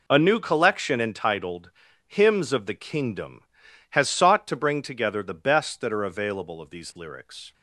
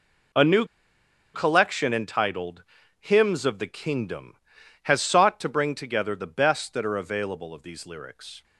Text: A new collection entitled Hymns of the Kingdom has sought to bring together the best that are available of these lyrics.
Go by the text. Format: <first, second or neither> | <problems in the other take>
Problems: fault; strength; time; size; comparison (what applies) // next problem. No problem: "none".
first | pauses between "new" and "collection"; noticeable; at 0.6 s; 0.69 s long // pauses between "entitled" and "Hymns"; slight; at 2.6 s; 0.34 s long; slight in the first